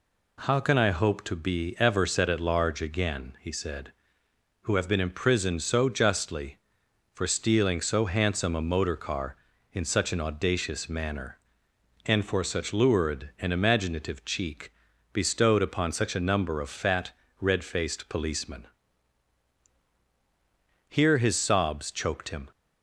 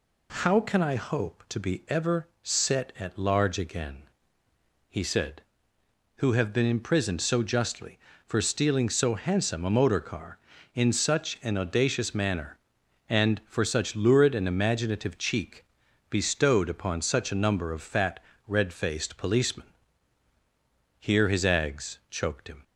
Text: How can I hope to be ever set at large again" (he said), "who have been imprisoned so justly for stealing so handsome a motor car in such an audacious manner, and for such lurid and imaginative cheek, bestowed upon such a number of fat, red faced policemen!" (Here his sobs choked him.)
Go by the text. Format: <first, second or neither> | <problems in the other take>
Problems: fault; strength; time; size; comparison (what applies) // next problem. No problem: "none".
first | says "ags" for "sobs"; at 21.4 s